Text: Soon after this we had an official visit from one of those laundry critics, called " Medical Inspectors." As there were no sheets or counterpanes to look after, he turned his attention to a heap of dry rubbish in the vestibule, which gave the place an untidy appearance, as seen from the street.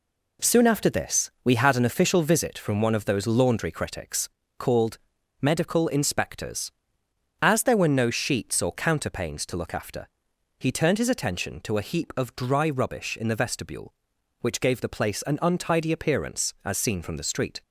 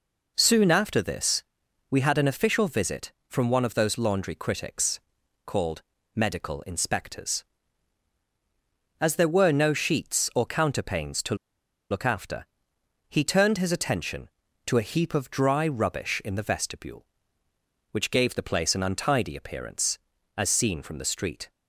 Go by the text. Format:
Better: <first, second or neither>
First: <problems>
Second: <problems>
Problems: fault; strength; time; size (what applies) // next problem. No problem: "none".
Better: first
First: none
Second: pauses between "this" and "we"; noticeable; at 1.4 s; 0.46 s long // pauses between "to" and "look"; noticeable; at 11.3 s; 0.54 s long